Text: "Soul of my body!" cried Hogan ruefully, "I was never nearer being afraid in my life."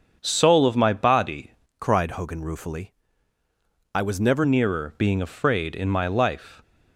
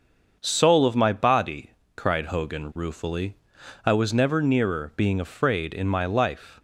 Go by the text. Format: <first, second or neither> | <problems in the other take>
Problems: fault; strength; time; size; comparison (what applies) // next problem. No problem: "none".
second | starts louder than the rest; until 1.2 s; 7 dB; also in the second // changes voice from "cried" to "never"; from 1.8 to 4.4 s; 2.6 s long